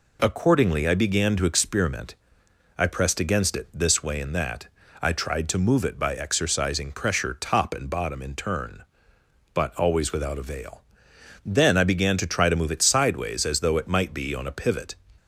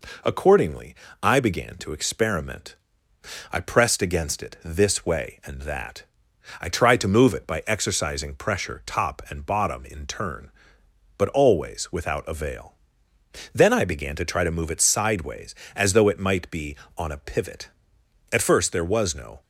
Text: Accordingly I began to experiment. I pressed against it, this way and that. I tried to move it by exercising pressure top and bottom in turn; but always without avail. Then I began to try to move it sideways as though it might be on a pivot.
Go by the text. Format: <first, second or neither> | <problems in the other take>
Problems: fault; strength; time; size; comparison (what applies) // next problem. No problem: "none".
first | pauses between "Accordingly" and "I"; slight; at 0.9 s; 0.28 s long // goes on to say "At first there was no"; noticeable; from 18.3 s on; 1.1 s long